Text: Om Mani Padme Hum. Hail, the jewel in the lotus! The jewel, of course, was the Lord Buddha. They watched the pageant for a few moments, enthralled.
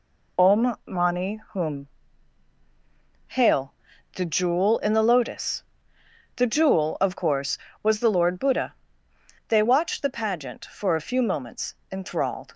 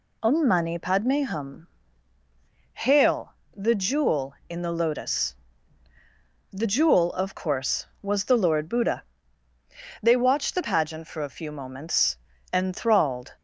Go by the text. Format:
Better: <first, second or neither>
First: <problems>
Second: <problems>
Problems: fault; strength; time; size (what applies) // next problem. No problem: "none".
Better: second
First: skips "Padme"; at 1.4 s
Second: none